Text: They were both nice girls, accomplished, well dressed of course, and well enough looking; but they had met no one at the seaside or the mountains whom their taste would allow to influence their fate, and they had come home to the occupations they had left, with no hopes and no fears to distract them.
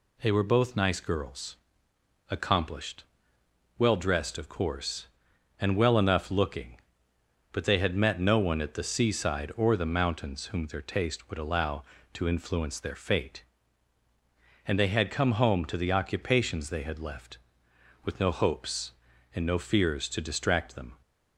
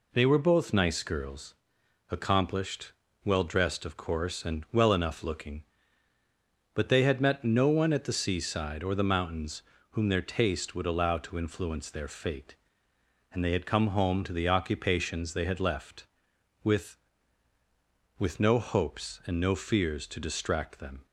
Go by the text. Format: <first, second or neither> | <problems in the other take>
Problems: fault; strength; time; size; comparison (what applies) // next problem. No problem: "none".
first | pauses between "mountains" and "whom"; slight; at 9.6 s; 0.28 s long // says "with" twice; at 18.1 s